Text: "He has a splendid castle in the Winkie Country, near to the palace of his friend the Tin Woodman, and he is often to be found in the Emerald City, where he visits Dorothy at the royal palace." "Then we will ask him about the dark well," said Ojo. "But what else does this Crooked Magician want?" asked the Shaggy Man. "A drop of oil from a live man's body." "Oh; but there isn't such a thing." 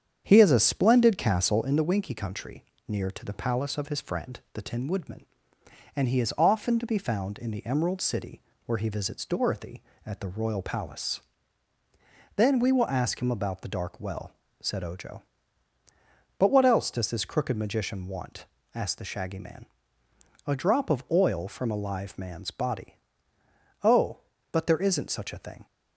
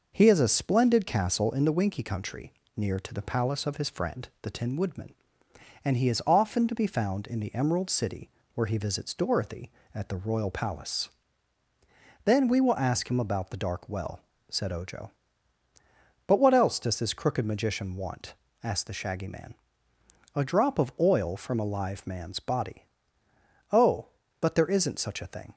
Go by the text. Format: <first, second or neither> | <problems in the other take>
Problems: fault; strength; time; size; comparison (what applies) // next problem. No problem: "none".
second | starts louder than the rest; strong; until 1.7 s; 8 dB